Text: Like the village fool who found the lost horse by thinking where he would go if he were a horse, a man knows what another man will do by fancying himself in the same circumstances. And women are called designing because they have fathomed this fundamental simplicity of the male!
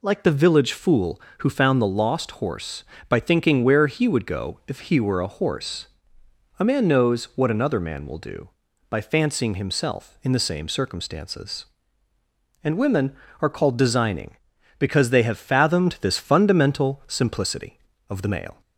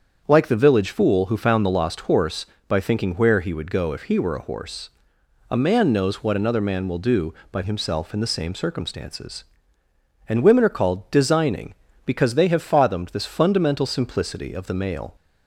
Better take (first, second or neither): first